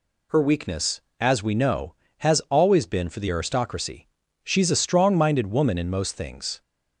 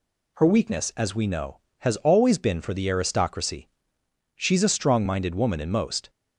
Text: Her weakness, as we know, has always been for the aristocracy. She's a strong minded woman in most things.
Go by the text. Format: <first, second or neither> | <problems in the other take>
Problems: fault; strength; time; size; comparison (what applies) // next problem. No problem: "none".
first | stops before "things"; at 6.0 s